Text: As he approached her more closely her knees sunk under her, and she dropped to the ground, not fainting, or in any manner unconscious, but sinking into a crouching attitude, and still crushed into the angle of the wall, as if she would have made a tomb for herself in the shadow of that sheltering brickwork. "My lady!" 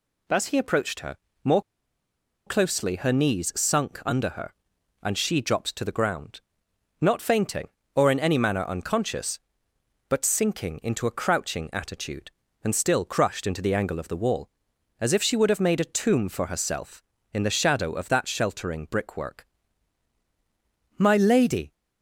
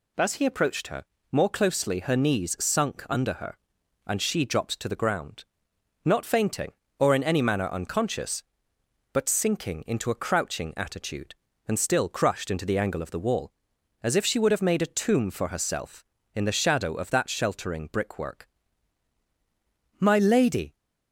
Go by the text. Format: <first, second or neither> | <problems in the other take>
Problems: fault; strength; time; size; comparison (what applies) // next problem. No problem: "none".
second | pauses between "her" and "more"; slight; at 1.1 s; 0.26 s long; slight in the second // pauses between "more" and "closely"; noticeable; at 1.6 s; 0.85 s long